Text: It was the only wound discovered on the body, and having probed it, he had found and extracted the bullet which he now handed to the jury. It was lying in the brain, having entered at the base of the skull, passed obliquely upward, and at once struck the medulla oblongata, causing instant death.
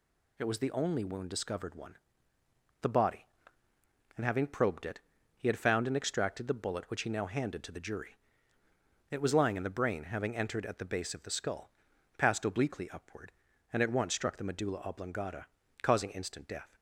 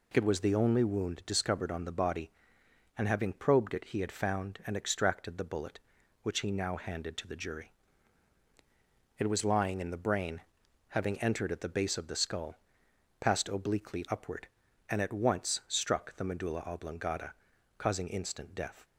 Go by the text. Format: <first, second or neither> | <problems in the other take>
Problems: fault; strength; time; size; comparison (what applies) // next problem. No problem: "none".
second | says "one" for "on"; at 1.7 s